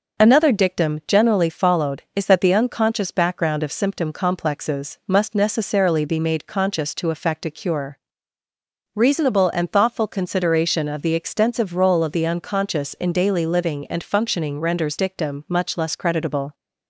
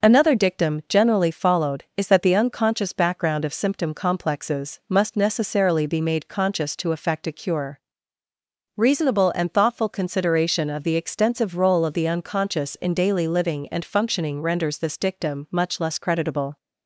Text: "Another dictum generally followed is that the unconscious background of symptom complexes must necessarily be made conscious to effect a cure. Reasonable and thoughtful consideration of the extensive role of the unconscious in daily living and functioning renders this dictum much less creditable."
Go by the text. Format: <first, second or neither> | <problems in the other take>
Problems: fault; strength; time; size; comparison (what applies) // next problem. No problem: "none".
second | skips "this"; at 14.9 s